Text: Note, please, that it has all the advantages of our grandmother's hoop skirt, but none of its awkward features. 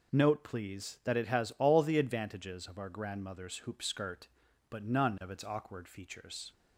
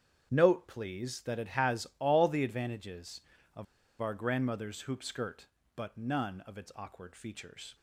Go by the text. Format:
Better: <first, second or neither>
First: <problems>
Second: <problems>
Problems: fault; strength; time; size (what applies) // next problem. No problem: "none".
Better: first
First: none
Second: starts louder than the rest; strong; until 1.3 s; 8.5 dB // pauses between "of" and "our"; slight; at 3.6 s; 0.35 s long